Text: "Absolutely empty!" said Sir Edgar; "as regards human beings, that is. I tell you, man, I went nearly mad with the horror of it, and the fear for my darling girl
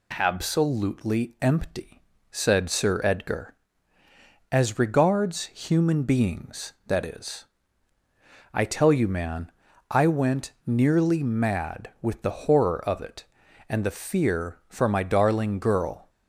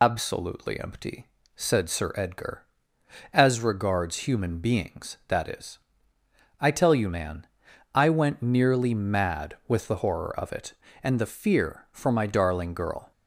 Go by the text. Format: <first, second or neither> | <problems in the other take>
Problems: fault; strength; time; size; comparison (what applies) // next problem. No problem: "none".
first | loses the start of "Absolutely"; at 0.0 s; 105 ms